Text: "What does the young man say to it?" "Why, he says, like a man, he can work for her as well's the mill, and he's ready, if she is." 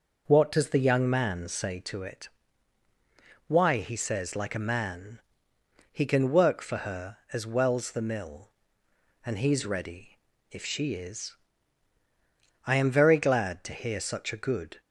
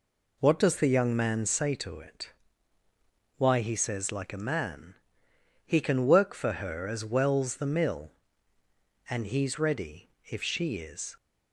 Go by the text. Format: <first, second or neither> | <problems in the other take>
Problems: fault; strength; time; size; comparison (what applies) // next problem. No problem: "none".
second | goes on to say "I am very glad to hear such a good"; strong; from 12.6 s on; 2.1 s long